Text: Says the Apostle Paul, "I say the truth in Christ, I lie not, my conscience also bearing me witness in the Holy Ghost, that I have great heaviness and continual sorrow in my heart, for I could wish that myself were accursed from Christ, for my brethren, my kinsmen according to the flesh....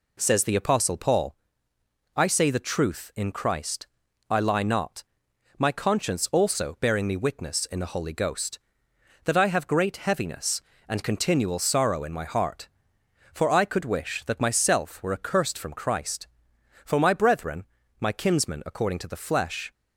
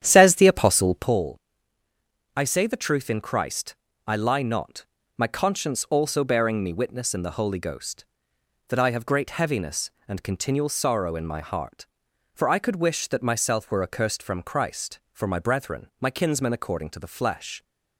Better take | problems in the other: first | starts louder than the rest; strong; until 1.2 s; 9.5 dB

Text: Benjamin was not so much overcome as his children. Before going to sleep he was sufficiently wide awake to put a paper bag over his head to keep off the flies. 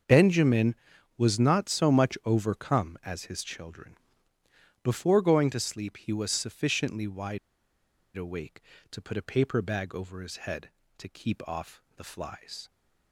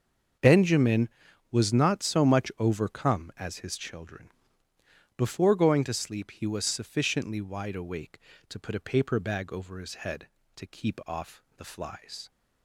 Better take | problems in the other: second | starts louder than the rest; until 1.4 s; 6.5 dB; also in the second // pauses between "wide" and "awake"; noticeable; at 7.3 s; 0.77 s long // pauses between "off" and "the"; slight; at 11.8 s; 0.16 s long; slight in the second

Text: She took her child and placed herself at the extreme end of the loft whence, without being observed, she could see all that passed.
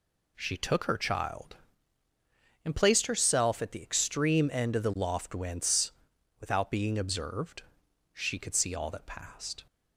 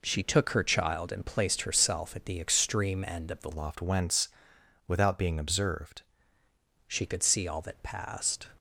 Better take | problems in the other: first | changes voice from "loft" to "observed"; from 3.5 to 6.0 s; 2.5 s long

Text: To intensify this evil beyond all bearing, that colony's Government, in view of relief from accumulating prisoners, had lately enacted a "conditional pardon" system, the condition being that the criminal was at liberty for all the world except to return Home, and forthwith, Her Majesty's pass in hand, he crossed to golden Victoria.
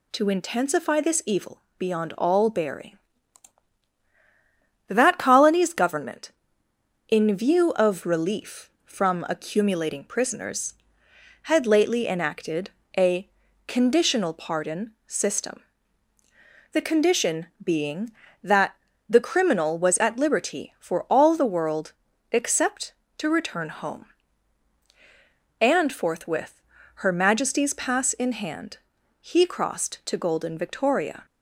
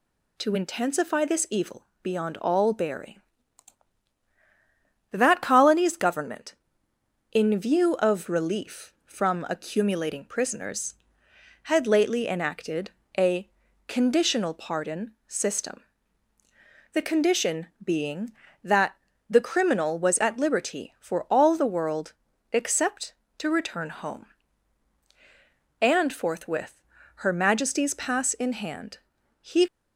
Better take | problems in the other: first | pauses between "evil" and "beyond"; slight; at 1.8 s; 0.18 s long; slight in the first // pauses between "enacted" and "a"; slight; at 12.9 s; 0.26 s long; slight in the first // pauses between "a" and "conditional"; at 13.4 s; 0.38 s long; also in the first // pauses between "pardon" and "system"; slight; at 15.1 s; 0.16 s long; slight in the first // pauses between "condition" and "being"; slight; at 17.6 s; 0.16 s long; slight in the first // pauses between "that" and "the"; slight; at 18.9 s; 0.34 s long; slight in the first // pauses between "world" and "except"; at 22.1 s; 0.38 s long; also in the first // stops before "crossed to golden Victoria"; at 29.6 s

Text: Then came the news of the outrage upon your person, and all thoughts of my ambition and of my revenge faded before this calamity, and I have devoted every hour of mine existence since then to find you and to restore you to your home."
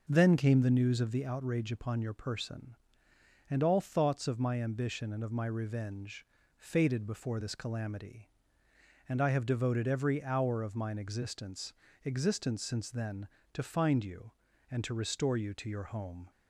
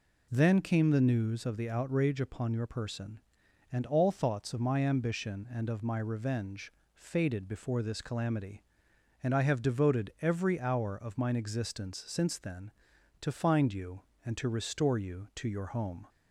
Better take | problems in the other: second | pauses between "revenge" and "faded"; slight; at 6.2 s; 0.30 s long; slight in the second // says "existence" twice; at 12.0 s

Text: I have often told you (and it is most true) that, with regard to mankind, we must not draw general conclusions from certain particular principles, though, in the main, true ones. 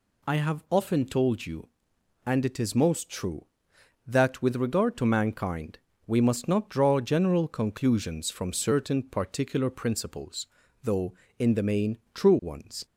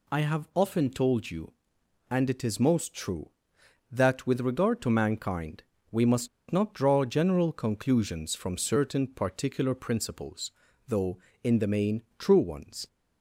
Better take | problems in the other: first | pauses between "must" and "not"; slight; at 6.2 s; 0.23 s long

